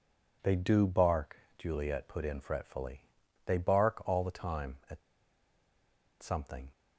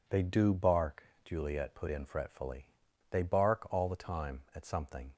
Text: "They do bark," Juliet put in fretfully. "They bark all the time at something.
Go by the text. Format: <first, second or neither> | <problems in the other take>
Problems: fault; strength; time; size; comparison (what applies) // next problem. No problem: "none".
second | pauses between "at" and "something"; at 4.9 s; 1.2 s long